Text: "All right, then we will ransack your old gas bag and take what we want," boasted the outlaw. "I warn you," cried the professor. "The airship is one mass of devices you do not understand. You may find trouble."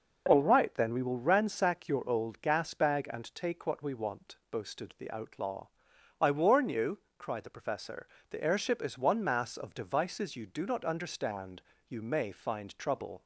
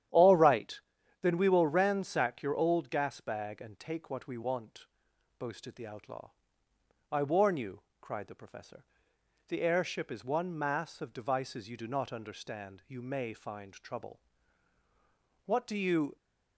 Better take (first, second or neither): first